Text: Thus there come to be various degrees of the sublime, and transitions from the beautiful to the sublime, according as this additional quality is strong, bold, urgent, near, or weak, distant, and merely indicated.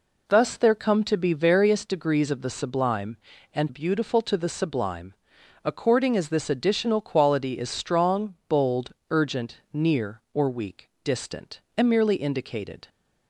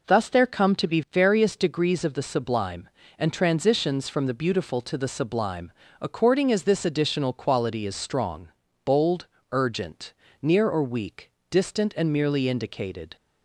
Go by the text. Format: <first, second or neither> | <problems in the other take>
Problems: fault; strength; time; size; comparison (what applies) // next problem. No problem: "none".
second | skips "transitions from the"; at 3.6 s